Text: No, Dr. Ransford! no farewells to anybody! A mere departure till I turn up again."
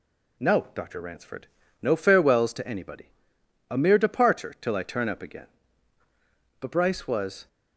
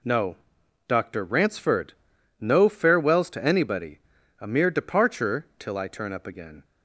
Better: second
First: goes on to say "But Bryce was"; noticeable; from 6.5 s on; 0.88 s long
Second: none

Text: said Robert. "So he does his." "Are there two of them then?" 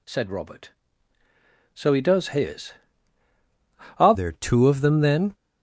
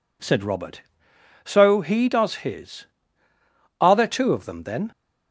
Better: second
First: changes voice at "there"; from 4.1 s on; 1.2 s long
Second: none

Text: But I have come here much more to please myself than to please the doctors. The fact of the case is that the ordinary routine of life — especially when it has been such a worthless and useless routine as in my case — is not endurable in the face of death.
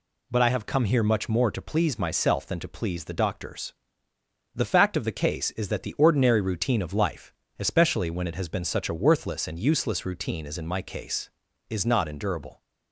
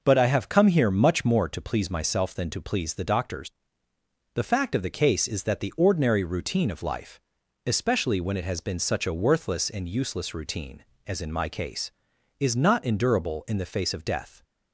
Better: second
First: stops before "in the face of death"; at 12.6 s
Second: none

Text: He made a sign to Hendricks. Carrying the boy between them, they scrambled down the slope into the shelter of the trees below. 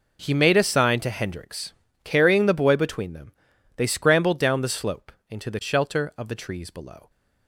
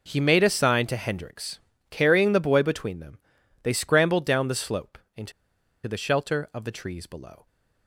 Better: first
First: pauses between "slope" and "into"; slight; at 5.1 s; 0.18 s long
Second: pauses between "slope" and "into"; slight; at 4.9 s; 0.18 s long // pauses between "into" and "the"; noticeable; at 5.3 s; 0.54 s long

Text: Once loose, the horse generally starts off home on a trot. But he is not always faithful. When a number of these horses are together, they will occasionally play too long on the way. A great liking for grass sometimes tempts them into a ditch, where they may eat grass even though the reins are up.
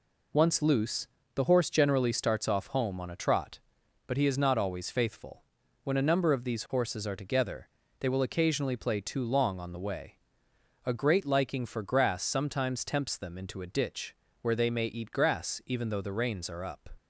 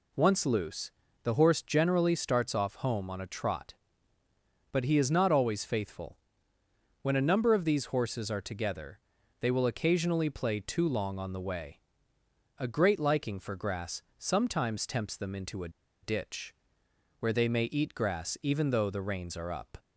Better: first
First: none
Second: pauses between "grass" and "sometimes"; slight; at 14.0 s; 0.16 s long // pauses between "a" and "ditch"; slight; at 15.6 s; 0.33 s long

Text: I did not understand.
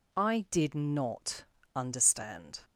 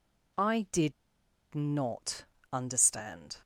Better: first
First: pauses between "not" and "understand"; slight; at 1.4 s; 0.31 s long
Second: pauses between "did" and "not"; noticeable; at 0.9 s; 0.61 s long // pauses between "not" and "understand"; slight; at 2.2 s; 0.28 s long

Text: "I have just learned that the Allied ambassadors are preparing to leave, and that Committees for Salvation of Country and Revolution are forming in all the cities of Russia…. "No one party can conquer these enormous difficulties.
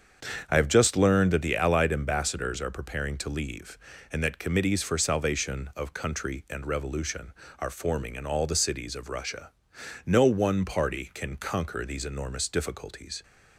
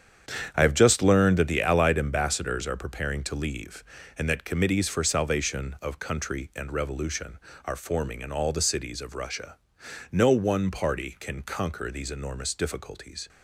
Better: first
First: starts louder than the rest; strong; until 1.5 s; 7 dB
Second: gets quieter; strong; throughout; 10 dB // starts louder than the rest; strong; until 1.5 s; 8 dB

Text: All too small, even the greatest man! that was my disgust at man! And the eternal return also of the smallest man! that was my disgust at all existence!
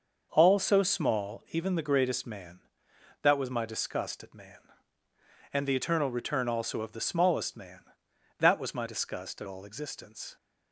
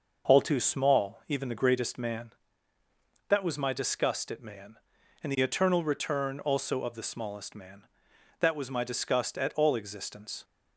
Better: second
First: starts louder than the rest; noticeable; until 1.3 s; 6 dB // says "so" for "too"; at 0.5 s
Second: none

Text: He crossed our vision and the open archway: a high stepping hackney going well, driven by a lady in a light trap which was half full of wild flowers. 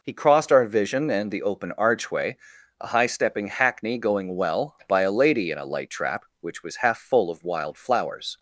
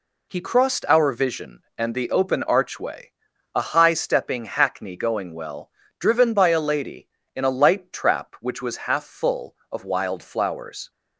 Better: second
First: skips "driven"; at 4.8 s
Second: none

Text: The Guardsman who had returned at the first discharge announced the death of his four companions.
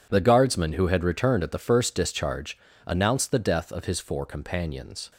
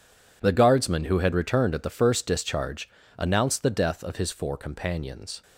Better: neither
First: pauses between "discharge" and "announced"; slight; at 2.5 s; 0.30 s long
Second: pauses between "discharge" and "announced"; slight; at 2.8 s; 0.30 s long

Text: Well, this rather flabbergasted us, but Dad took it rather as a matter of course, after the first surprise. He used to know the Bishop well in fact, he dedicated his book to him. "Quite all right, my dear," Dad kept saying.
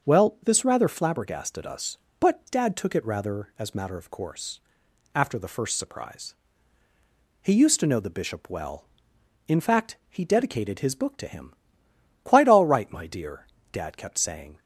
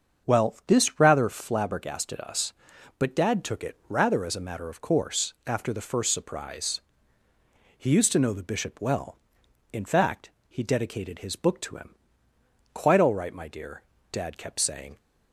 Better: second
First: starts louder than the rest; until 1.1 s; 6.5 dB // skips "a"; at 3.7 s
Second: starts louder than the rest; until 1.3 s; 7 dB

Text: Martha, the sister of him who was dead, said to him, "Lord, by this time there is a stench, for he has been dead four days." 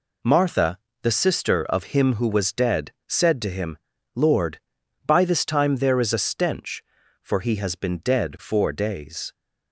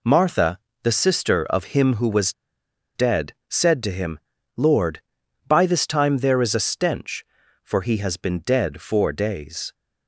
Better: first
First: none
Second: pauses between "was" and "dead"; noticeable; at 2.3 s; 0.63 s long

